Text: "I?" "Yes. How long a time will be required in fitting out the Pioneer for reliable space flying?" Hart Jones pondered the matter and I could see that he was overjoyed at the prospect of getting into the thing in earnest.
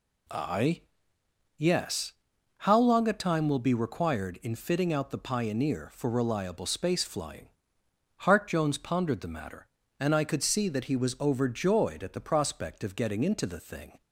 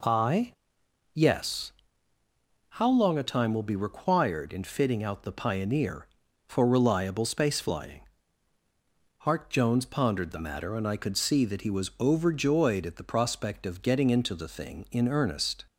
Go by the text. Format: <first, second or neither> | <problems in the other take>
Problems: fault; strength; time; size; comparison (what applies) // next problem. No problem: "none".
second | stops before "in earnest"; at 14.0 s